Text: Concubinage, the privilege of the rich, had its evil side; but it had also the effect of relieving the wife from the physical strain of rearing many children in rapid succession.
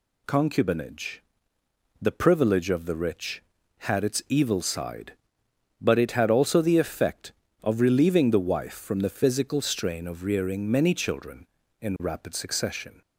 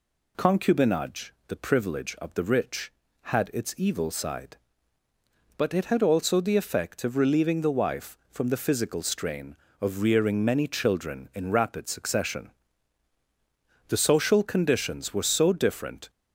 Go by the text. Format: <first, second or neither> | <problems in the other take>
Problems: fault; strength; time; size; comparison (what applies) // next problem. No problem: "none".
first | goes on to say "The social conditions were so different"; strong; from 13.8 s on; 2.2 s long